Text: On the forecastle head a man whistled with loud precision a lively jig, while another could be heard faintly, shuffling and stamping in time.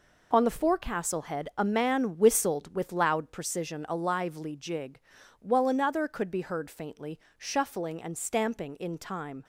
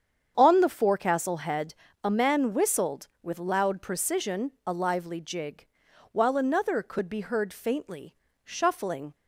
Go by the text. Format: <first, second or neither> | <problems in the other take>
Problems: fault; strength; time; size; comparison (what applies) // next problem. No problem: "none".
first | starts louder than the rest; strong; until 1.3 s; 8 dB // pauses between "head" and "a"; slight; at 1.7 s; 0.28 s long // pauses between "precision" and "a"; slight; at 4.5 s; 0.16 s long // stops before "and stamping in time"; at 9.1 s